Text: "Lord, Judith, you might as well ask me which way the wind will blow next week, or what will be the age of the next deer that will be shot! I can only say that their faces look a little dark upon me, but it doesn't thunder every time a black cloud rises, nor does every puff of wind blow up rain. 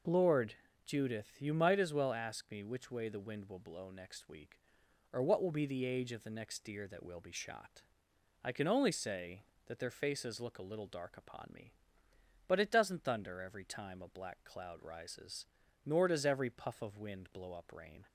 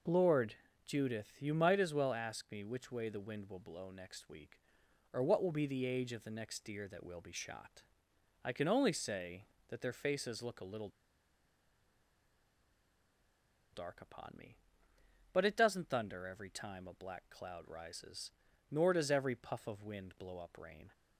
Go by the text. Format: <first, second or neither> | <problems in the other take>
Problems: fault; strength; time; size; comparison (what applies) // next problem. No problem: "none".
first | pauses between "little" and "dark"; strong; at 10.8 s; 2.8 s long